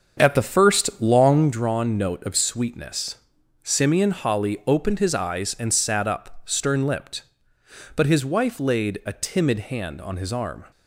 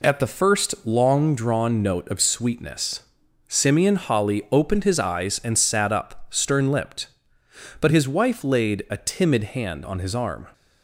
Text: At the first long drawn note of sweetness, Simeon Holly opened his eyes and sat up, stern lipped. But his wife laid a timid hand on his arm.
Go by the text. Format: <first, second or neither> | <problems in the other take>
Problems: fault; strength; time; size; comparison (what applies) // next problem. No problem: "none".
second | starts louder than the rest; until 1.6 s; 6.5 dB